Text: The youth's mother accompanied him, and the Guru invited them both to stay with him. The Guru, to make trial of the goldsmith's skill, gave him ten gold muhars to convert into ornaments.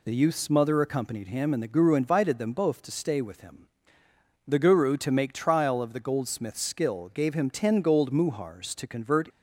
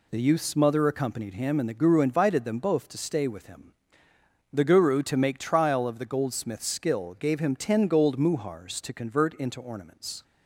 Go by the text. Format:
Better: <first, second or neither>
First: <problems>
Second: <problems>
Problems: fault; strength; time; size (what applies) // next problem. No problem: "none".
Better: second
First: stops before "into ornaments"; at 9.2 s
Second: none